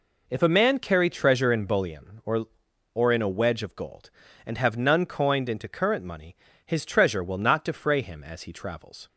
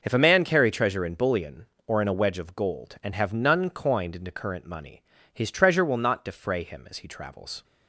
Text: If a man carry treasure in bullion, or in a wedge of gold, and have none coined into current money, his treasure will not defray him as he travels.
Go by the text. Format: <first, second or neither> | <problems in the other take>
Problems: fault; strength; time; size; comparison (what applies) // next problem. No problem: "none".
second | says "or" twice; at 2.9 s